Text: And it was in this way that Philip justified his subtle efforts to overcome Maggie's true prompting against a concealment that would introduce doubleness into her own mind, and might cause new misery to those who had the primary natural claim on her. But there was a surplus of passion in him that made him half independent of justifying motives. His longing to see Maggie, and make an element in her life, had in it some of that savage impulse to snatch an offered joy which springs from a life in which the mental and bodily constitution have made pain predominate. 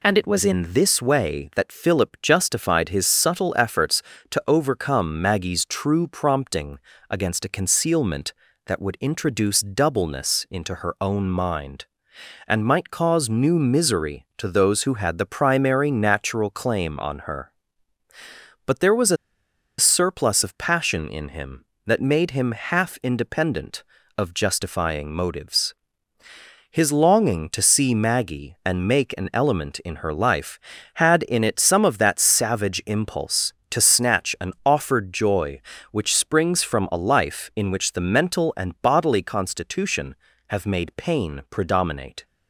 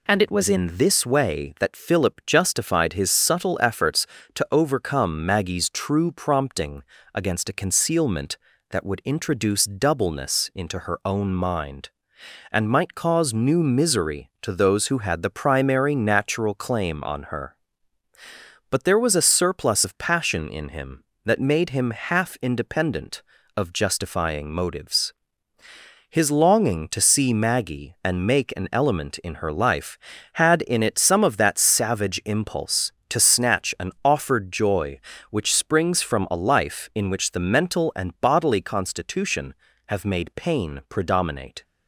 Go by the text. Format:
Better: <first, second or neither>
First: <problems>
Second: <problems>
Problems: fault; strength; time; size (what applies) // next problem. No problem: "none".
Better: second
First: pauses between "prompting" and "against"; slight; at 6.7 s; 0.30 s long // pauses between "a" and "surplus"; noticeable; at 19.1 s; 0.62 s long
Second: pauses between "prompting" and "against"; slight; at 6.8 s; 0.30 s long